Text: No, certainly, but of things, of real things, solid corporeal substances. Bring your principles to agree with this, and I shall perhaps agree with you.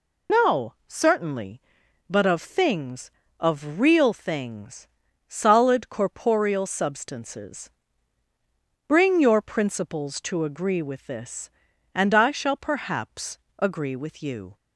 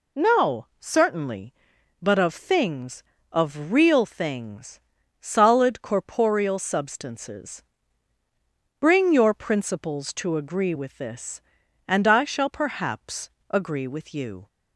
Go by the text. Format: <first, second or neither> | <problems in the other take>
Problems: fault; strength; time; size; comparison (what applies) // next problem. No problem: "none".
second | loses the start of "No"; at 0.2 s; 65 ms // pauses between "perhaps" and "agree"; slight; at 13.3 s; 0.20 s long; slight in the second